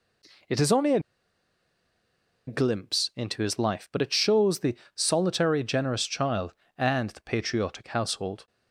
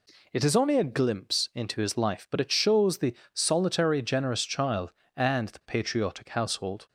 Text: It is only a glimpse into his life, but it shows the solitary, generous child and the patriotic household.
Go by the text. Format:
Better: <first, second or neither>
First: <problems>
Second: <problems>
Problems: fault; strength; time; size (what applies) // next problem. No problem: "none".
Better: second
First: pauses between "a" and "glimpse"; strong; at 0.9 s; 1.4 s long // pauses between "the" and "solitary"; slight; at 4.7 s; 0.18 s long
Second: pauses between "the" and "solitary"; slight; at 3.1 s; 0.18 s long